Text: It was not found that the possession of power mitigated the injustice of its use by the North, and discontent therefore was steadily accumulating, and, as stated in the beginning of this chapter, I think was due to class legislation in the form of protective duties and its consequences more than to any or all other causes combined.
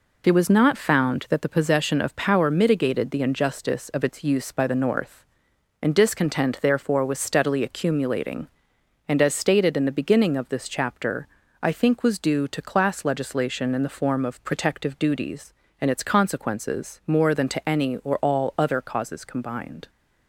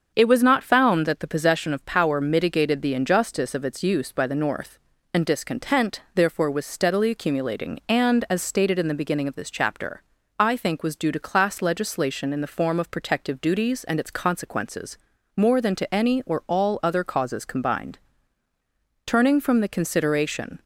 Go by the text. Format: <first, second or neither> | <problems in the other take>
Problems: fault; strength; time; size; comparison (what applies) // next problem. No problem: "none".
first | starts louder than the rest; until 1.1 s; 7 dB // pauses between "consequences" and "more"; slight; at 14.9 s; 0.36 s long // goes on to say "Turning from the consideration"; from 19.0 s on; 1.5 s long